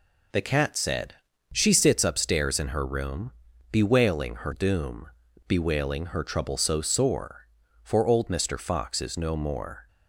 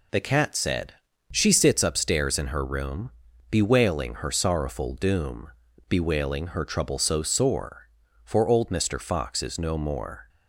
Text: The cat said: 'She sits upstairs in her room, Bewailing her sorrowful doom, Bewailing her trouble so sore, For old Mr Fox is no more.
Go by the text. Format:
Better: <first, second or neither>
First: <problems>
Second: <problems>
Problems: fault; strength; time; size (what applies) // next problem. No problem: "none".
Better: second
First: skips "sorrowful"; at 4.5 s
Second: none